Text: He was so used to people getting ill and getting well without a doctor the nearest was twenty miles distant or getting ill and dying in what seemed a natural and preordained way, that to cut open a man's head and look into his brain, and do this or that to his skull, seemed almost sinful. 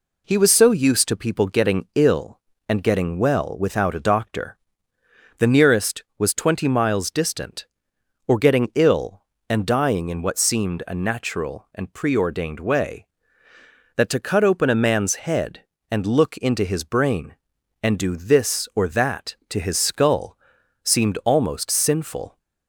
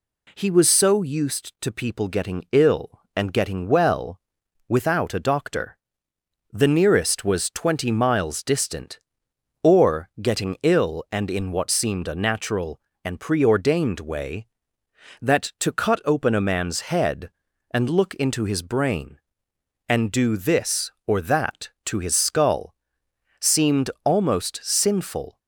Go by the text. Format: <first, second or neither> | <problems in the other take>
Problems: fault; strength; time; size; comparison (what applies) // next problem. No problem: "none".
first | pauses between "well" and "without"; noticeable; at 4.1 s; 0.48 s long // pauses between "doctor" and "the"; noticeable; at 5.7 s; 0.74 s long; noticeable in the first // skips "dying"; at 11.2 s // pauses between "seemed" and "almost"; slight; at 23.8 s; 0.16 s long